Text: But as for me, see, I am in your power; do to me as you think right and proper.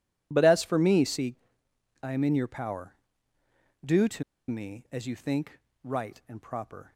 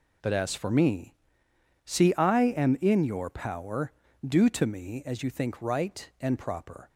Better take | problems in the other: second | pauses between "to" and "me"; slight; at 4.2 s; 0.25 s long // pauses between "think" and "right"; slight; at 5.5 s; 0.24 s long

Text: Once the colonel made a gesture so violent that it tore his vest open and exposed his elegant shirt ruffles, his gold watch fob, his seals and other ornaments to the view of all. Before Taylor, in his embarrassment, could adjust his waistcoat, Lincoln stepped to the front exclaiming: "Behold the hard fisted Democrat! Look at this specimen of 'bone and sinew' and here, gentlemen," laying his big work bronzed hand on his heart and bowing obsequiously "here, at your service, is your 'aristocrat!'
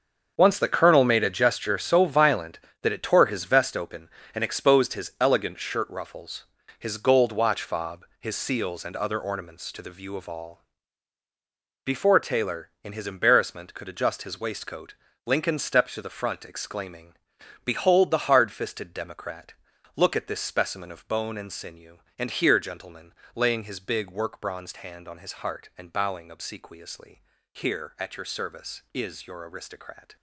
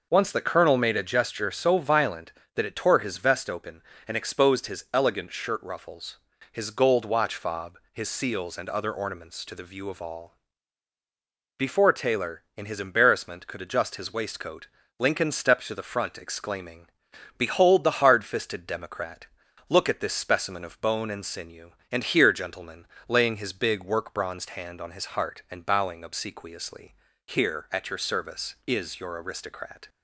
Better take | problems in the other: second | gets quieter; strong; throughout; 11.5 dB // pauses between "obsequiously" and "here"; slight; at 27.2 s; 0.32 s long; slight in the second

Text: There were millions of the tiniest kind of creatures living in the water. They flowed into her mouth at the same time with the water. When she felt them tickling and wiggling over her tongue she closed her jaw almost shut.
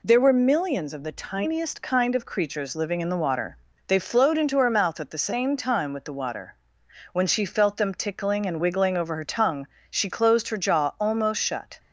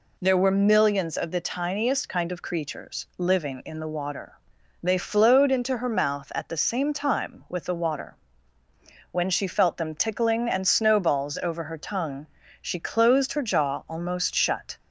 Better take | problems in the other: first | says "snowballs" for "wiggling"; at 10.6 s // pauses between "tongue" and "she"; slight; at 12.2 s; 0.34 s long; slight in the first

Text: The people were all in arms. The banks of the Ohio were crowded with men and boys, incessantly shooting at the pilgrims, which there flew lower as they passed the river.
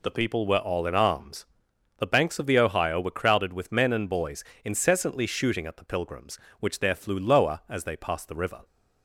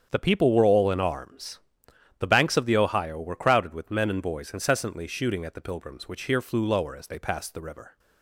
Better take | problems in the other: first | starts louder than the rest; strong; until 1.1 s; 8 dB // says "here" for "there"; at 6.2 s

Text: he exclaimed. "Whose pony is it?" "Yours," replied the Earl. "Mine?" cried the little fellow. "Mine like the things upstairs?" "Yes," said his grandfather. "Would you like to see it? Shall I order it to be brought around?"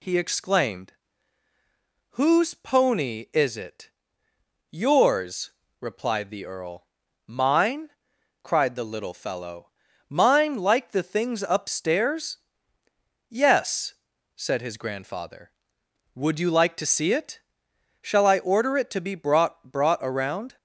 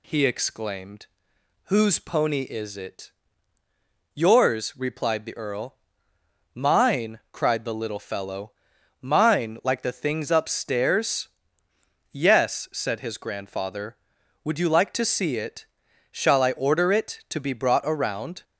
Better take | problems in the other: second | says "brought" twice; at 19.7 s

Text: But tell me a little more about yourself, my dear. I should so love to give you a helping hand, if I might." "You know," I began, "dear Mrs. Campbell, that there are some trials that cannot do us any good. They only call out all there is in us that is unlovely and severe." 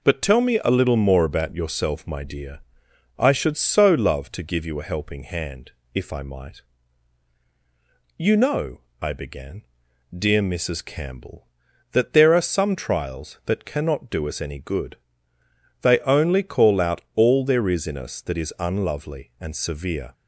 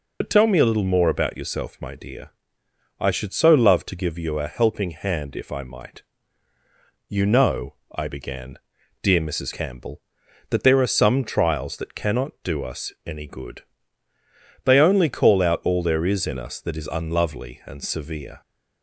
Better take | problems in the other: first | loses the start of "But"; at 0.2 s; 50 ms // pauses between "us" and "any"; slight; at 12.9 s; 0.16 s long

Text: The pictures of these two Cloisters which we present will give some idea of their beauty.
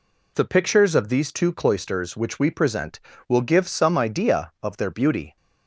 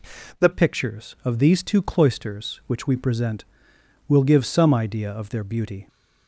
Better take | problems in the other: first | changes voice at "pictures"; from 0.5 s on; 5.3 s long

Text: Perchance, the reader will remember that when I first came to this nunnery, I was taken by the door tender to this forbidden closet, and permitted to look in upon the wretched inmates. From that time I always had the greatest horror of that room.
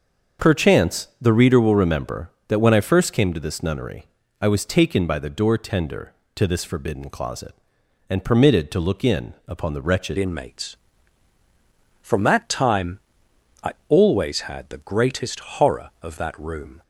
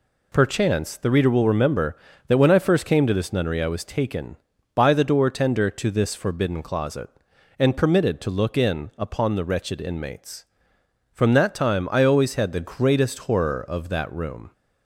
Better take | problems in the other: second | starts louder than the rest; until 1.5 s; 6 dB // changes voice at "inmates"; from 10.1 s on; 6.7 s long // pauses between "time" and "I"; noticeable; at 12.9 s; 0.64 s long // pauses between "I" and "always"; slight; at 13.7 s; 0.16 s long

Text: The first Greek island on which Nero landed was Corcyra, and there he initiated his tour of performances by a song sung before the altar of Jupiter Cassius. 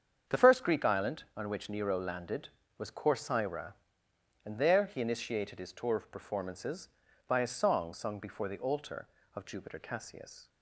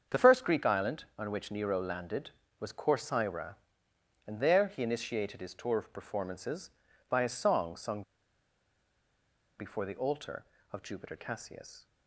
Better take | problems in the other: first | starts louder than the rest; strong; until 1.2 s; 7.5 dB; strong in the first // pauses between "sung" and "before"; strong; at 8.0 s; 1.5 s long

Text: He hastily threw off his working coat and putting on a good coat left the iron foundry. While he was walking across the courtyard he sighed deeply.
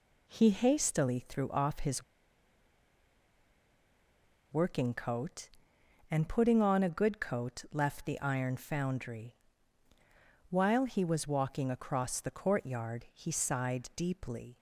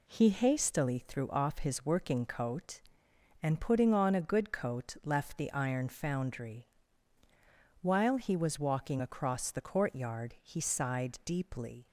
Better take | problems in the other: second | pauses between "his" and "working"; strong; at 2.0 s; 2.4 s long

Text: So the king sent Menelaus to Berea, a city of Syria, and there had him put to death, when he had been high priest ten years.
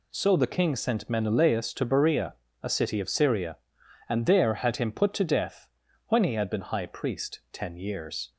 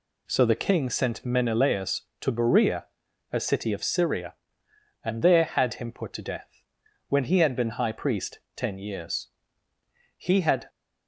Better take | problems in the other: first | pauses between "priest" and "ten"; slight; at 8.3 s; 0.20 s long // goes on to say "He had"; from 10.1 s on; 0.52 s long

